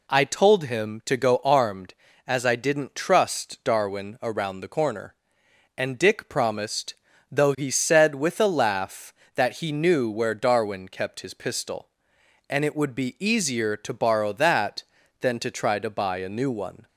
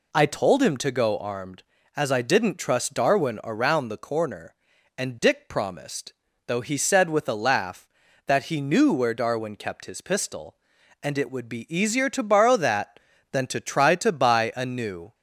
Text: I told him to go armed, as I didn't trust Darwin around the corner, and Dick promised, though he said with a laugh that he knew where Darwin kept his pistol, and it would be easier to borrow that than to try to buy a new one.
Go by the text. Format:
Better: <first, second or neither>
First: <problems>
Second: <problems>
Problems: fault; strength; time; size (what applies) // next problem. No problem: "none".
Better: first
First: none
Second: stops before "one"; at 15.1 s